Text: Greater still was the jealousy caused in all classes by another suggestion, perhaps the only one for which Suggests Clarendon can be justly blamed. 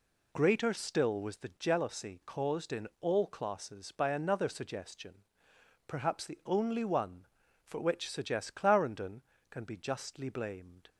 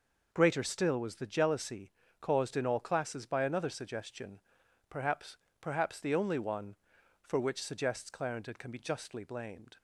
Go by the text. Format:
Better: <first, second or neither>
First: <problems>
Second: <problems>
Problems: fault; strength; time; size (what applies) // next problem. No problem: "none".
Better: first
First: none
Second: pauses between "jealousy" and "caused"; slight; at 1.9 s; 0.30 s long // says "perhaps" twice; at 5.5 s